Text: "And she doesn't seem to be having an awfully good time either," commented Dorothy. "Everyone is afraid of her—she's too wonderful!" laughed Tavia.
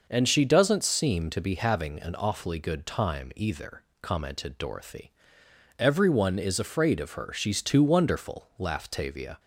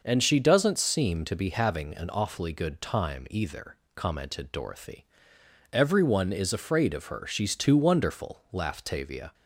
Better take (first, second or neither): neither